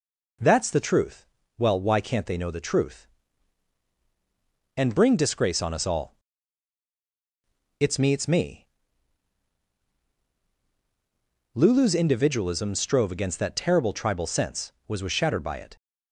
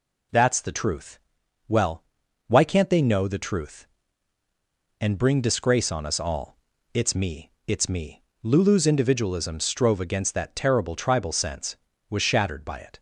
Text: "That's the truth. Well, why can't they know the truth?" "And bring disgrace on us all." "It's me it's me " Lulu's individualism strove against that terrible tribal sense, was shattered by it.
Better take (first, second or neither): second